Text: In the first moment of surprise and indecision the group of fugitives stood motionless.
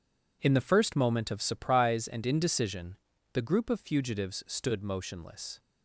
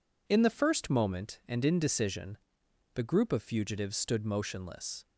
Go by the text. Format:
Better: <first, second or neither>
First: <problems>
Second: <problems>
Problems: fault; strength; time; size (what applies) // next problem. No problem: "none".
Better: first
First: pauses between "indecision" and "the"; at 2.9 s; 0.38 s long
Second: skips "of surprise"; at 1.4 s // pauses between "indecision" and "the"; noticeable; at 2.3 s; 0.58 s long